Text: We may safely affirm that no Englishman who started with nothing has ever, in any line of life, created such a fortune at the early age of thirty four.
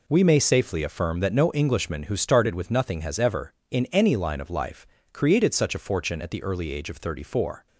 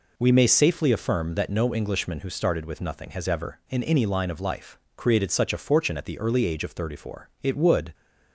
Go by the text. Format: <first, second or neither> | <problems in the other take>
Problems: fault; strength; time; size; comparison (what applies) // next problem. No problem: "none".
first | goes on to say "It would"; from 7.4 s on; 0.50 s long